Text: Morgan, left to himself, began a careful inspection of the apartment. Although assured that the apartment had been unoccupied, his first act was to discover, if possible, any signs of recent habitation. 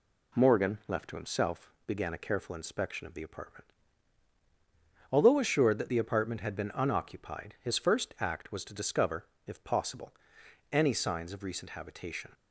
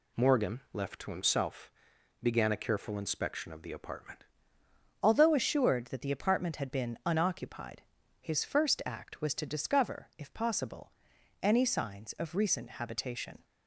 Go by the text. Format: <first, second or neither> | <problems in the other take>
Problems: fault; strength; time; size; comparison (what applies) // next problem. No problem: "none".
first | changes voice at "Although"; from 5.0 s on; 8.4 s long